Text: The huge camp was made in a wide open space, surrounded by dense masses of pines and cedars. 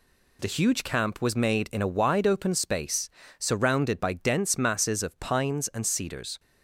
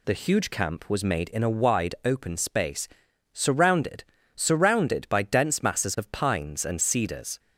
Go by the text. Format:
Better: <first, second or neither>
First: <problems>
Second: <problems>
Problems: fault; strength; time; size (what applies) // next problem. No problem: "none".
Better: first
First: none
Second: says "surrounded" twice; at 4.3 s